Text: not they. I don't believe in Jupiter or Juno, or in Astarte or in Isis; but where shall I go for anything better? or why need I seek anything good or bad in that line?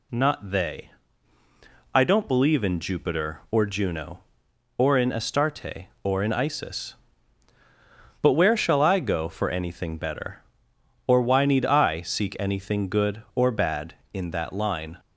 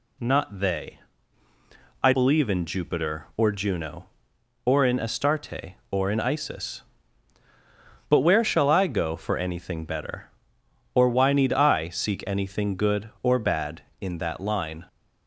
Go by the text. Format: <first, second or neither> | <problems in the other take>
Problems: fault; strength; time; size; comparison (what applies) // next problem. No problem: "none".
first | skips "don't"; at 2.1 s